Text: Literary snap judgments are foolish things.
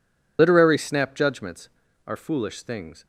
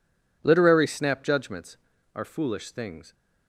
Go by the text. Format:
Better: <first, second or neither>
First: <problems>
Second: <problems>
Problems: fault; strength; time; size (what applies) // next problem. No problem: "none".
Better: second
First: loses the start of "Literary"; at 0.3 s; 70 ms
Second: none